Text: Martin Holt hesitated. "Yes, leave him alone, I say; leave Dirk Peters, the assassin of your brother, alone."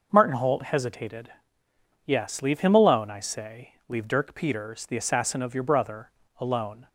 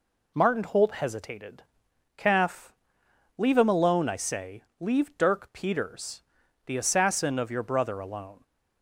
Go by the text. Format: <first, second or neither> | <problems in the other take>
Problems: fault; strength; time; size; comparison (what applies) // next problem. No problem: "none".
first | says "Calf" for "Yes"; at 2.1 s